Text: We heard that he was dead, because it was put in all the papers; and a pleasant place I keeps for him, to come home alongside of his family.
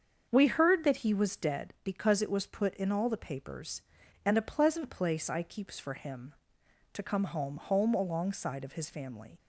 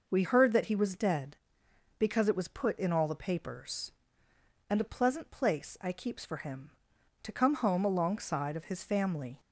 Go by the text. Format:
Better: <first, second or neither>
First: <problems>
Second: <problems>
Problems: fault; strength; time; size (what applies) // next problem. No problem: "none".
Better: second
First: starts louder than the rest; until 1.3 s; 7 dB // says "home" twice; at 7.5 s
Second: none